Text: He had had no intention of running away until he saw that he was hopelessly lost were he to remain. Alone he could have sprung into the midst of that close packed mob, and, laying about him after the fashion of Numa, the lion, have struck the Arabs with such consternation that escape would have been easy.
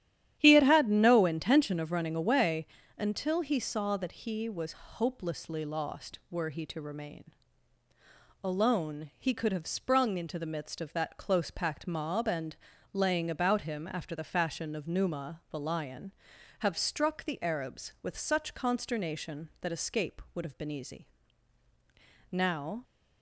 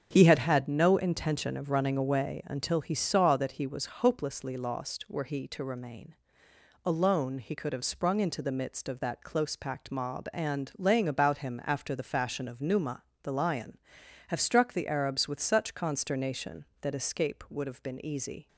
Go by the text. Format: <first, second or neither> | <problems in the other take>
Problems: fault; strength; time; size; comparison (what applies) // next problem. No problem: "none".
second | starts louder than the rest; strong; until 1.4 s; 11 dB; also in the second // pauses between "away" and "until"; slight; at 2.6 s; 0.28 s long // goes on to say "Now"; from 22.3 s on; 0.52 s long